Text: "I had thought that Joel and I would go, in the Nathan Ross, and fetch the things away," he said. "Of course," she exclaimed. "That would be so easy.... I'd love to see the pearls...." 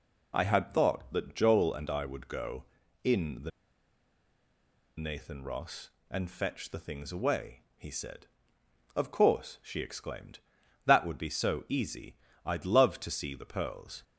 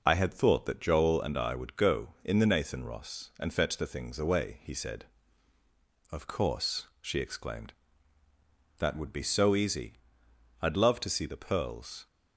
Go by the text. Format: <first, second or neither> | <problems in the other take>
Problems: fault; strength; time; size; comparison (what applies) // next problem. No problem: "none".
second | pauses between "the" and "Nathan"; strong; at 3.5 s; 1.4 s long